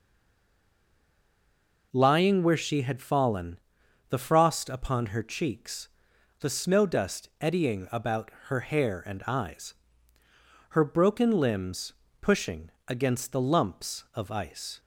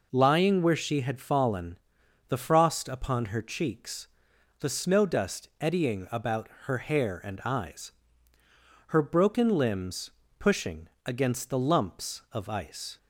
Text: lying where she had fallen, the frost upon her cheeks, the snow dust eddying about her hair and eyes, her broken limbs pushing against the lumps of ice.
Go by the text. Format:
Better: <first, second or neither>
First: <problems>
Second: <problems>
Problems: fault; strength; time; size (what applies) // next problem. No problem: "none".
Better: second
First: stays silent before the first word; noticeable; until 1.9 s; 1.9 s long // pauses between "about" and "her"; slight; at 8.2 s; 0.18 s long // pauses between "limbs" and "pushing"; slight; at 11.9 s; 0.30 s long // pauses between "pushing" and "against"; slight; at 12.6 s; 0.18 s long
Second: pauses between "about" and "her"; slight; at 6.4 s; 0.18 s long // pauses between "limbs" and "pushing"; slight; at 10.0 s; 0.30 s long // pauses between "pushing" and "against"; slight; at 10.8 s; 0.18 s long